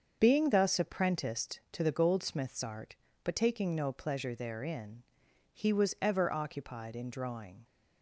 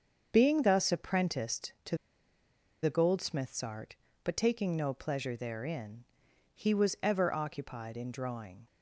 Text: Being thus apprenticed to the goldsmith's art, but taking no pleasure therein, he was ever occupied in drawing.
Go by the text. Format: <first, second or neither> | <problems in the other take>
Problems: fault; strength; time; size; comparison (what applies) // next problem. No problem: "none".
first | starts louder than the rest; until 1.3 s; 7 dB; also in the first // pauses between "to" and "the"; noticeable; at 1.9 s; 0.85 s long